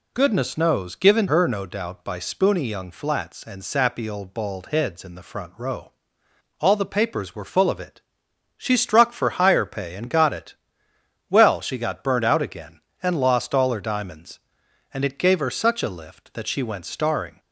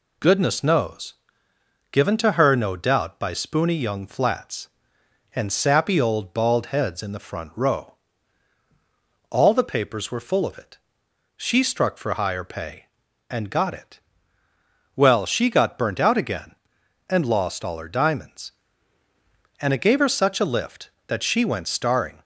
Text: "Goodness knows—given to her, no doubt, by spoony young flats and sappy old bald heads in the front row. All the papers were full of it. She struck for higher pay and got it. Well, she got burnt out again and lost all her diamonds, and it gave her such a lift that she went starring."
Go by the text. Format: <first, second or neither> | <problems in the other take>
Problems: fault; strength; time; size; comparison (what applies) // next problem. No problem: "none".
second | skips "to"; at 1.2 s